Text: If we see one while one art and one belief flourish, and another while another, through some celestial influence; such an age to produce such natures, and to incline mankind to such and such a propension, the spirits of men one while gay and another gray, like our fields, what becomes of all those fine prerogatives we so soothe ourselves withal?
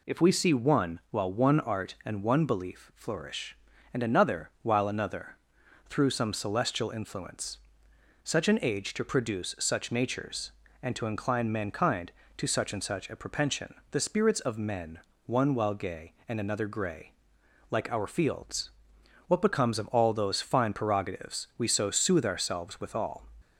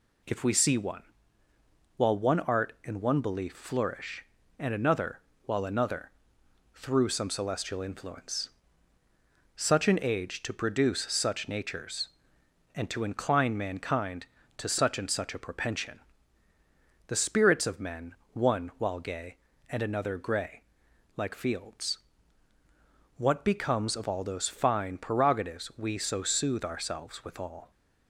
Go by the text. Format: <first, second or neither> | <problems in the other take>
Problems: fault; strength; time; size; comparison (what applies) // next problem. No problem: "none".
first | pauses between "one" and "while"; noticeable; at 1.0 s; 0.94 s long // pauses between "another" and "while"; slight; at 5.1 s; 0.26 s long // pauses between "men" and "one"; slight; at 18.1 s; 0.16 s long; slight in the first // skips "our"; at 21.3 s